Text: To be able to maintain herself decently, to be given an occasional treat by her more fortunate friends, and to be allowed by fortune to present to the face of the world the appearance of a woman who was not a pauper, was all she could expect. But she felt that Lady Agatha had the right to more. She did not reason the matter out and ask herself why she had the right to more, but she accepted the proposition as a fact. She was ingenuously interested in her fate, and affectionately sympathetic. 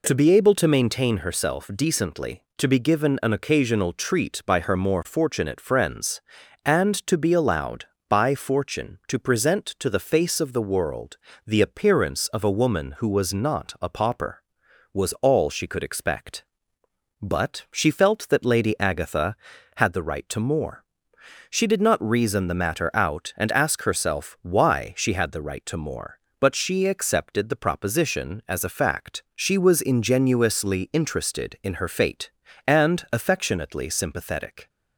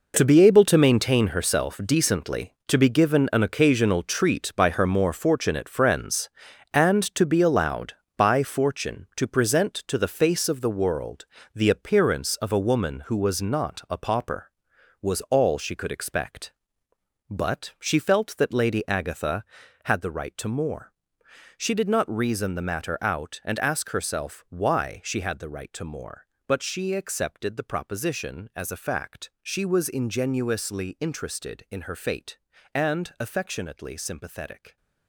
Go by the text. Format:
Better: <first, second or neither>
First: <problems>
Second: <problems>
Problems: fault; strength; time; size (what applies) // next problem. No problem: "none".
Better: first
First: pauses between "world" and "the"; slight; at 11.1 s; 0.28 s long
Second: gets quieter; strong; throughout; 12 dB // pauses between "world" and "the"; slight; at 11.2 s; 0.28 s long